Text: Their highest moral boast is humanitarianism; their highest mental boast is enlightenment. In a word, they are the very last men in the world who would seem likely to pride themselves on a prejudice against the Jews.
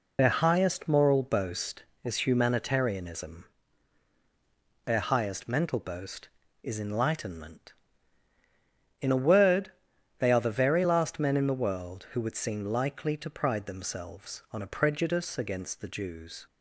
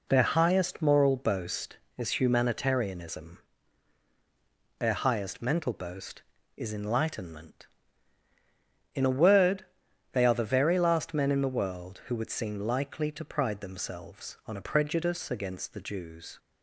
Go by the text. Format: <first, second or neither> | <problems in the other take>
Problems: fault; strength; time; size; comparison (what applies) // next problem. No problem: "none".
second | loses the start of "Their"; at 0.1 s; 35 ms